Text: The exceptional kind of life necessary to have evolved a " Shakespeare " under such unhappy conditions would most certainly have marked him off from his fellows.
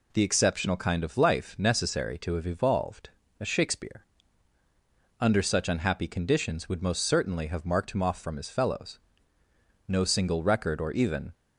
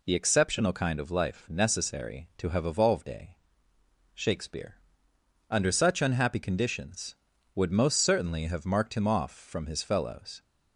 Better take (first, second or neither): second